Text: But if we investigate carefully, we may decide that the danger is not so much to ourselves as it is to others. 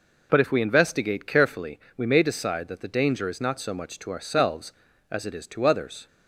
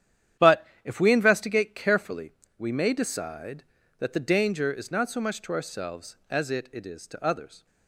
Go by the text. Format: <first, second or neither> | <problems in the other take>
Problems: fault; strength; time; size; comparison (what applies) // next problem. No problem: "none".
first | starts louder than the rest; strong; until 1.5 s; 10 dB // pauses between "But" and "if"; slight; at 0.6 s; 0.18 s long // says "it" twice; at 6.7 s